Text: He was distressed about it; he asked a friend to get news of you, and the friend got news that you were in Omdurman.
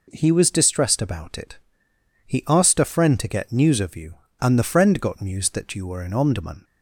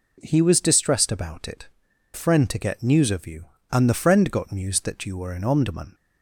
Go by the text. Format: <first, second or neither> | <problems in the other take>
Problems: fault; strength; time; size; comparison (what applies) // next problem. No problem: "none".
first | skips "he asked a"; at 1.9 s